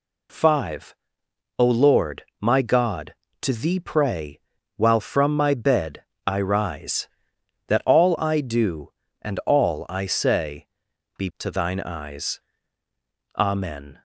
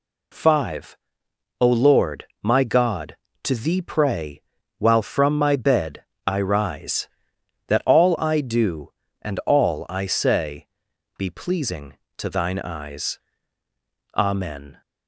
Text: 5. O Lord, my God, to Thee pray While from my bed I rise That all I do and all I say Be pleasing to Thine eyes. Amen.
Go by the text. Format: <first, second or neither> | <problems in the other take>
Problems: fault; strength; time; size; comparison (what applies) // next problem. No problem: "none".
second | pauses between "pray" and "While"; at 4.3 s; 0.38 s long; also in the second // pauses between "bed" and "I"; slight; at 6.0 s; 0.22 s long; slight in the second // pauses between "say" and "Be"; noticeable; at 10.6 s; 0.50 s long; noticeable in the second // skips "pleasing"; at 11.3 s